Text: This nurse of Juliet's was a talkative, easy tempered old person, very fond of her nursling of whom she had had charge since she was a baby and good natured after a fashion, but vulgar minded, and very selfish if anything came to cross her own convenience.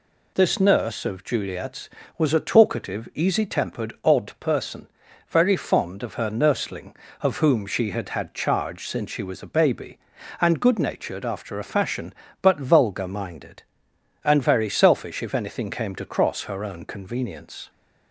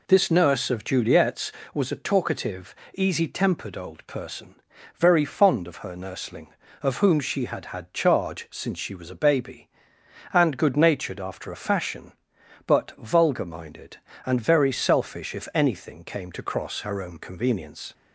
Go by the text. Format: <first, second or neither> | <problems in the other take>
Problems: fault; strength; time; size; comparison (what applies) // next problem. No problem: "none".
second | says "odd" for "old"; at 4.0 s